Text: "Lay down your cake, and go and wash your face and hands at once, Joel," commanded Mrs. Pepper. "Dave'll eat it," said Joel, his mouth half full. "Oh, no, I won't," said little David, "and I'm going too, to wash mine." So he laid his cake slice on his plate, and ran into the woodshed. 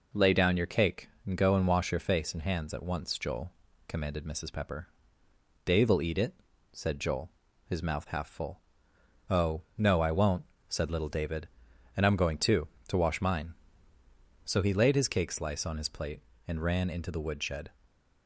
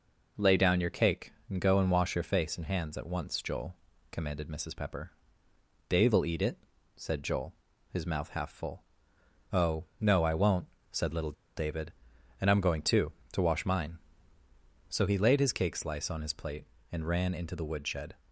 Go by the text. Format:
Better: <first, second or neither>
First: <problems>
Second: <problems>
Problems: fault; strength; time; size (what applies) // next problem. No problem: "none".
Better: first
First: none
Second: pauses between "little" and "David"; slight; at 11.3 s; 0.24 s long